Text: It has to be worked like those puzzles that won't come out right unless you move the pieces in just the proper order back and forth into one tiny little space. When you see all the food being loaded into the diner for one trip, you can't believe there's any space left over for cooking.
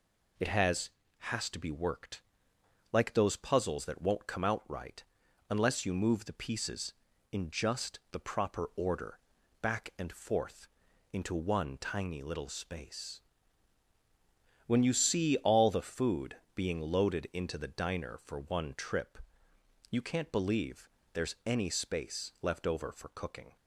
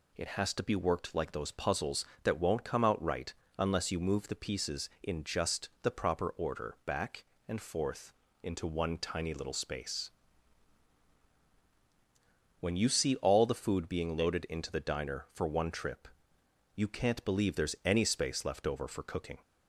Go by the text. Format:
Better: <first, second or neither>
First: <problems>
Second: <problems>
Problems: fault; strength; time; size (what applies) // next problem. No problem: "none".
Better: second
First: says "has" twice; at 1.1 s // pauses between "worked" and "like"; noticeable; at 2.2 s; 0.70 s long // pauses between "right" and "unless"; noticeable; at 5.0 s; 0.48 s long // pauses between "order" and "back"; at 9.1 s; 0.42 s long // pauses between "forth" and "into"; at 10.6 s; 0.44 s long // pauses between "food" and "being"; slight; at 16.3 s; 0.18 s long // pauses between "believe" and "there's"; slight; at 20.8 s; 0.26 s long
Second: pauses between "right" and "unless"; slight; at 3.3 s; 0.26 s long // pauses between "forth" and "into"; slight; at 8.1 s; 0.30 s long